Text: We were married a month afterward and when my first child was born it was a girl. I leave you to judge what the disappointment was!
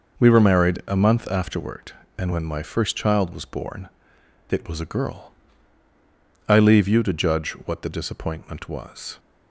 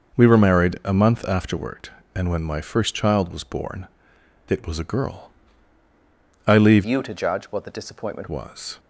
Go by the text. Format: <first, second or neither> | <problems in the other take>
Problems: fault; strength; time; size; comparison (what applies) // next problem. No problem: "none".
first | pauses between "born" and "it"; noticeable; at 3.8 s; 0.60 s long; noticeable in the first // changes voice from "you" to "disappointment"; from 6.8 to 8.2 s; 1.4 s long